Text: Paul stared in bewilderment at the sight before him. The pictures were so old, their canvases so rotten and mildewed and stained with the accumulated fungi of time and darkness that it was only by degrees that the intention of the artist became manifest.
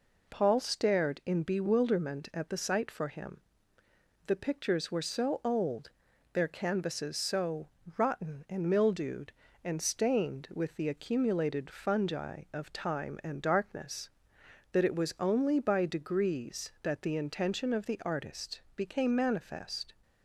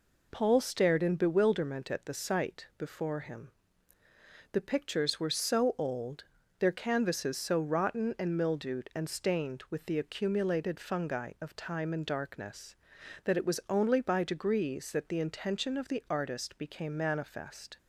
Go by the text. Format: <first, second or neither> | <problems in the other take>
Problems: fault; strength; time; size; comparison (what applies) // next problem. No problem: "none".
second | says "for" for "before"; at 2.9 s // pauses between "so" and "rotten"; slight; at 7.6 s; 0.28 s long